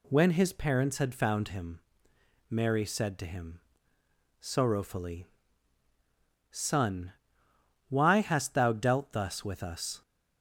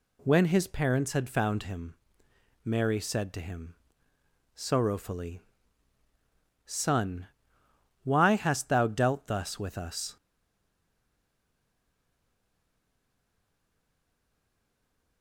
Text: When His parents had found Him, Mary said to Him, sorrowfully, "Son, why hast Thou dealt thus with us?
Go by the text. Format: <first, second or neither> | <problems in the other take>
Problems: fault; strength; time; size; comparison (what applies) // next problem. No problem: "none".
first | stays silent after the last word; strong; from 10.1 s on; 5.1 s long